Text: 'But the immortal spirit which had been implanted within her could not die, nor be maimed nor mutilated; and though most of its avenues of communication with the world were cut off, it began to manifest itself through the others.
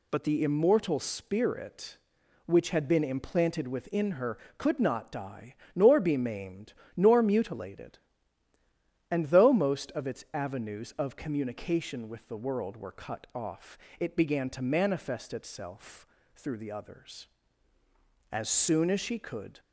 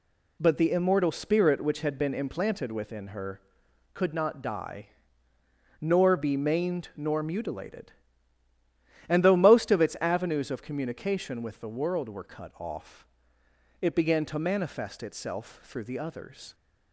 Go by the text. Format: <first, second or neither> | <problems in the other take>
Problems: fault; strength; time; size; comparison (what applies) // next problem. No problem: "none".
second | pauses between "maimed" and "nor"; slight; at 6.7 s; 0.24 s long // pauses between "itself" and "through"; slight; at 16.0 s; 0.29 s long // goes on to say "As soon as she could"; noticeable; from 18.3 s on; 1.2 s long